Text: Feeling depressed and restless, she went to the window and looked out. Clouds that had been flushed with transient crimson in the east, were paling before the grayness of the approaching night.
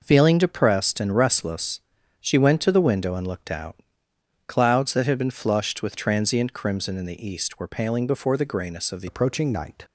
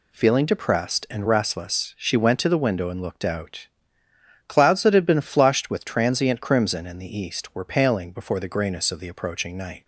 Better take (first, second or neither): second